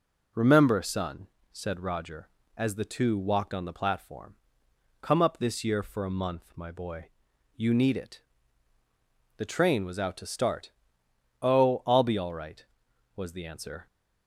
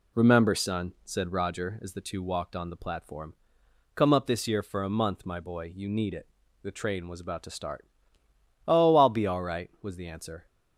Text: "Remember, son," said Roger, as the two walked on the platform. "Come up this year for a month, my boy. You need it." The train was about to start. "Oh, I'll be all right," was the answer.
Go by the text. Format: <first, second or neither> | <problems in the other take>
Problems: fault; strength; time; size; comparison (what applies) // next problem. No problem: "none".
second | says "out" for "about"; at 9.9 s